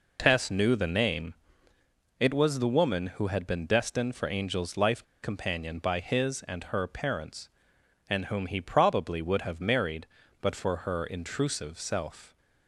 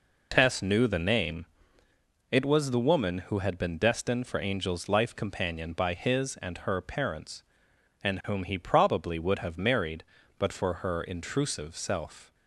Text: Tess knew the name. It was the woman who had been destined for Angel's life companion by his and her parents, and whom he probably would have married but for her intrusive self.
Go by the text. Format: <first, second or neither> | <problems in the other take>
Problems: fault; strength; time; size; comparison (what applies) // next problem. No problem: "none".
second | pauses between "life" and "companion"; slight; at 5.0 s; 0.19 s long